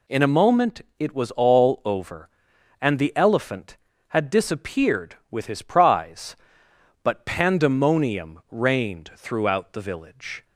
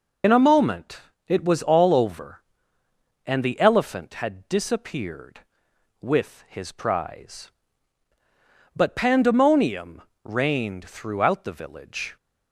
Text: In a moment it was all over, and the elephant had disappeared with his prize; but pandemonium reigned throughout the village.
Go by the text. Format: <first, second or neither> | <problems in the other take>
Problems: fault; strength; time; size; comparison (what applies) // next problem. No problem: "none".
first | loses the start of "In"; at 0.2 s; 40 ms // pauses between "moment" and "it"; slight; at 0.9 s; 0.30 s long; slight in the first // pauses between "pandemonium" and "reigned"; slight; at 10.0 s; 0.22 s long